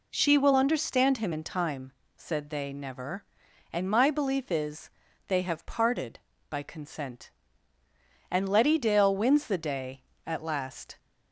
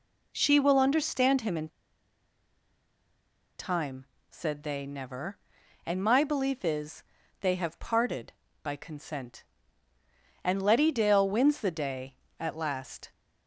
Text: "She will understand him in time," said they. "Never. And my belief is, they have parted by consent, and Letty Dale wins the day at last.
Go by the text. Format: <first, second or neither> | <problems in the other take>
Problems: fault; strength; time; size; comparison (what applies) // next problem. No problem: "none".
first | pauses between "in" and "time"; strong; at 1.6 s; 1.9 s long